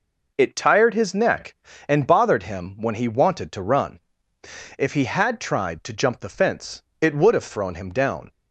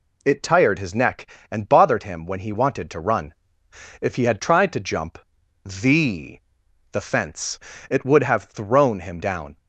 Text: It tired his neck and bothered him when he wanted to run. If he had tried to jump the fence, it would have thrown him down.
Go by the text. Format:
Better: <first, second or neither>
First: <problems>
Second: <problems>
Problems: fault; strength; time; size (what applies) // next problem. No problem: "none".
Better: first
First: none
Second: pauses between "jump" and "the"; noticeable; at 5.1 s; 0.46 s long // says "the" twice; at 6.9 s